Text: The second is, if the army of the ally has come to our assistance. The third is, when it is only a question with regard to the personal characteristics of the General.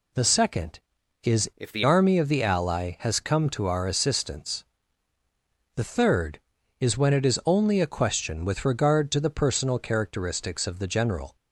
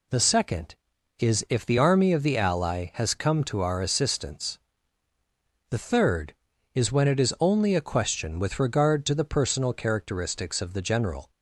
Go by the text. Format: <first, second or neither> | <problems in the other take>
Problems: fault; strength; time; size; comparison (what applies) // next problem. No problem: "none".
second | changes voice from "if" to "the"; from 1.5 to 1.8 s; 0.3 s long